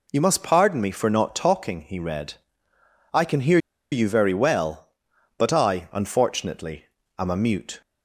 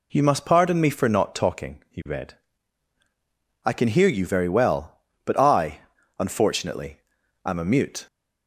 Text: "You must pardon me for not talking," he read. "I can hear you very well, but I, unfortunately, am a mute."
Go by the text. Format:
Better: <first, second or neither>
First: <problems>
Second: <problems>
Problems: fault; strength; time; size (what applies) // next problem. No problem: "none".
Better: second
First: pauses between "hear" and "you"; slight; at 3.5 s; 0.34 s long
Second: none